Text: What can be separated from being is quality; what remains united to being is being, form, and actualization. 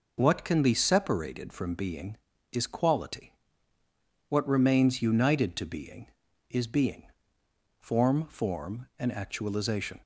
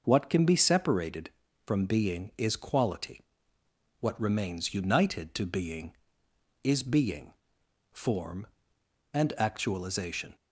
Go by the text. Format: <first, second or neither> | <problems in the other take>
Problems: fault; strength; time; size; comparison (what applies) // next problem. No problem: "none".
second | says "form" twice; at 8.2 s